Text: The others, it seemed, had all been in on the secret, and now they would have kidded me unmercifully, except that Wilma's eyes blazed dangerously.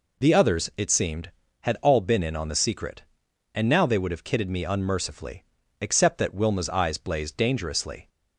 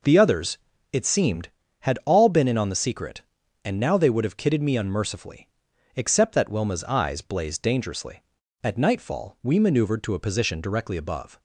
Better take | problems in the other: first | goes on to say "At nightfall we maneuvered to a position directly above"; strong; from 8.6 s on; 2.7 s long

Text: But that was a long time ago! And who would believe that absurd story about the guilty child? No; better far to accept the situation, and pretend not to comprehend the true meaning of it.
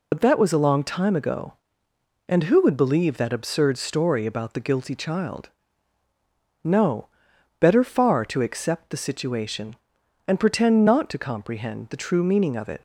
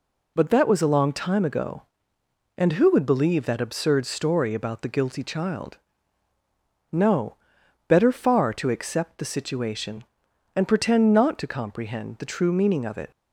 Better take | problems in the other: second | loses the start of "But"; at 0.1 s; 55 ms

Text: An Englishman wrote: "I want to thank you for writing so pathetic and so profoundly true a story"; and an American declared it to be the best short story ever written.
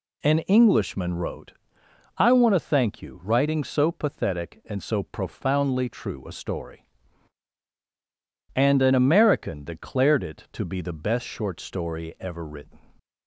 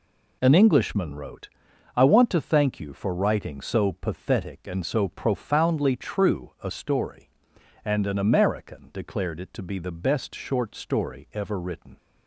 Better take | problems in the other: second | skips "for"; at 3.2 s

